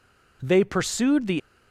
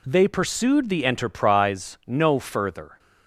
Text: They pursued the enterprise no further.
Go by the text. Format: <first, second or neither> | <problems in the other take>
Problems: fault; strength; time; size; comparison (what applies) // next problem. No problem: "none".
second | stops before "enterprise no further"; at 1.3 s